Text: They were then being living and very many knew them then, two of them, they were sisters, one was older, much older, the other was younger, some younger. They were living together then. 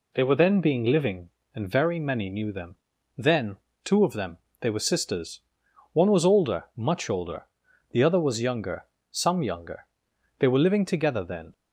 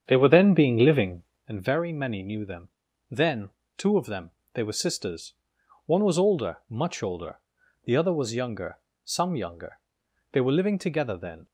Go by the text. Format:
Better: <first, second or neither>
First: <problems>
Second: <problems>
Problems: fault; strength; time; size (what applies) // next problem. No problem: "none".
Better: first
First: pauses between "them" and "then"; at 2.7 s; 0.40 s long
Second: starts louder than the rest; strong; until 1.5 s; 8 dB // pauses between "them" and "then"; at 2.6 s; 0.40 s long